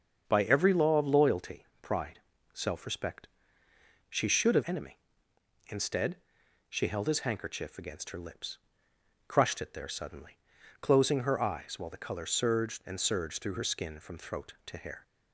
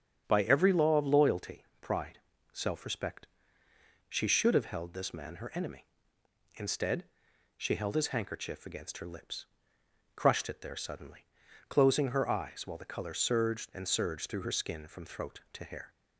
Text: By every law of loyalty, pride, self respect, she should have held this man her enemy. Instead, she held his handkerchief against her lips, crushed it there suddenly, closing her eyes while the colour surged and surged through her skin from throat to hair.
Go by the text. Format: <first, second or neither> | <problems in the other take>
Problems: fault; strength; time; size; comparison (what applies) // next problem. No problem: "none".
second | starts louder than the rest; strong; until 1.3 s; 7 dB; strong in the second // skips "held this man her"; at 4.6 s